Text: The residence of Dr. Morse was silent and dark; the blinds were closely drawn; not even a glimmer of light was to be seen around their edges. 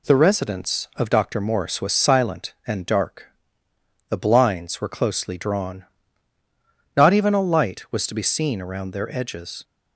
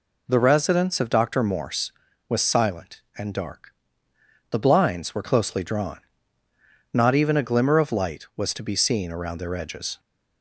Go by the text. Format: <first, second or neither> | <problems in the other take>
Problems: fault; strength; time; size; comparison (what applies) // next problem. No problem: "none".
second | skips "glimmer of"; at 7.4 s